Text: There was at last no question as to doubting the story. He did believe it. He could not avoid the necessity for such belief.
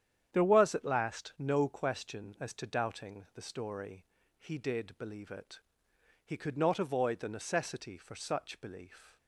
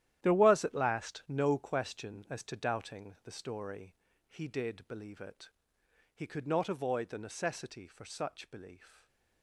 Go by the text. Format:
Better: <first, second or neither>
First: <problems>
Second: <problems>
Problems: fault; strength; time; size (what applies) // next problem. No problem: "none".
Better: first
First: starts louder than the rest; strong; until 1.3 s; 9.5 dB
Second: gets quieter; strong; throughout; 12.5 dB // starts louder than the rest; strong; until 1.2 s; 12 dB // stays silent after the last word; slight; from 8.8 s on; 0.6 s long